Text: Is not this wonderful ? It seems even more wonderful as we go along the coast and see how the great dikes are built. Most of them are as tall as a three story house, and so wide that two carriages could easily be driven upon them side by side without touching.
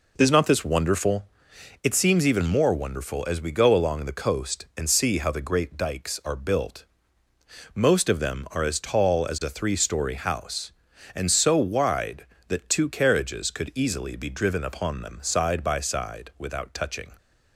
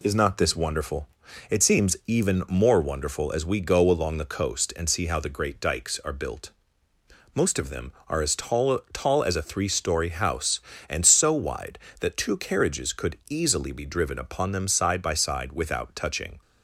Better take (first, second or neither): first